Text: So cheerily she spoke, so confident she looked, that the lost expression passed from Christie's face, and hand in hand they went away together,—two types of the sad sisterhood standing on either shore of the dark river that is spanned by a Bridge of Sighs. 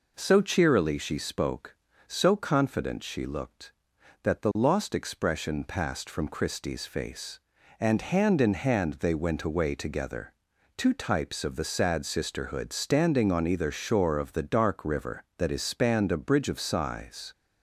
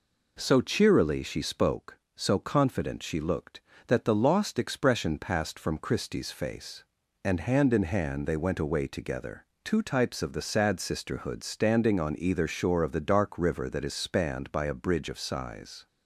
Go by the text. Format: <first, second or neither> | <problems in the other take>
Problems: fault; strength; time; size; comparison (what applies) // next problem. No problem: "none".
second | skips "by"; at 16.1 s